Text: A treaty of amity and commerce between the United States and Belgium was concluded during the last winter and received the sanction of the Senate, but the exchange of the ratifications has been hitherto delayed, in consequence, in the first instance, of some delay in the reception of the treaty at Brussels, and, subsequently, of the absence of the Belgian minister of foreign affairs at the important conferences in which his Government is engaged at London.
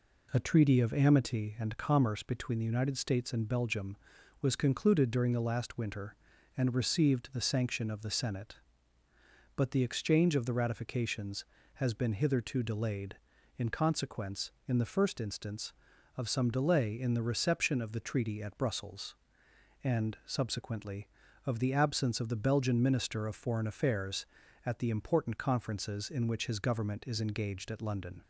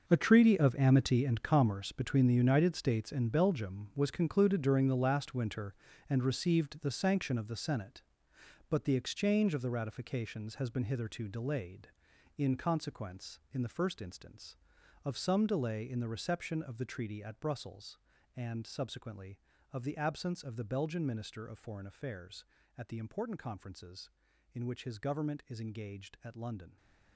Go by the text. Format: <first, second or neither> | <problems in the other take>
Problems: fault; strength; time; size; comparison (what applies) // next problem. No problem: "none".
first | gets quieter; strong; throughout; 13 dB